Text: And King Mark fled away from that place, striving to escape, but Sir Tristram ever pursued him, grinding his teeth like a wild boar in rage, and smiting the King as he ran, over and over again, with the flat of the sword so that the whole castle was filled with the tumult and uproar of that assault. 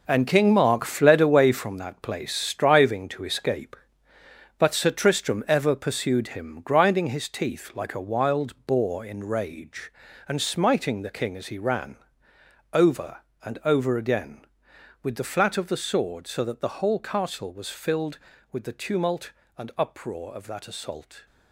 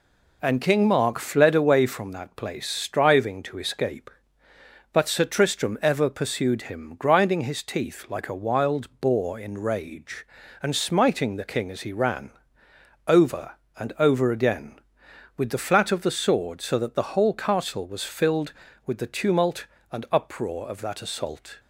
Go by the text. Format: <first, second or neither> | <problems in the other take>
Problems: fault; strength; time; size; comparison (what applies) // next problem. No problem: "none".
second | gets quieter; strong; throughout; 10.5 dB